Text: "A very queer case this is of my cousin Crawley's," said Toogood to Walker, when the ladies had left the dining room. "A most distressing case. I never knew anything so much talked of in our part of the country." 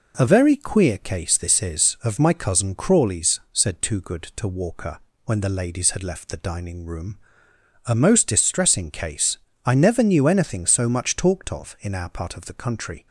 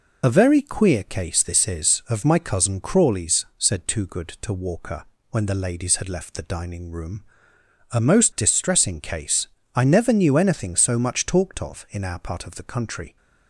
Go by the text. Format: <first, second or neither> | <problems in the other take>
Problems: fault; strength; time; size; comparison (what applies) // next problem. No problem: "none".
first | loses the start of "A"; at 0.2 s; 50 ms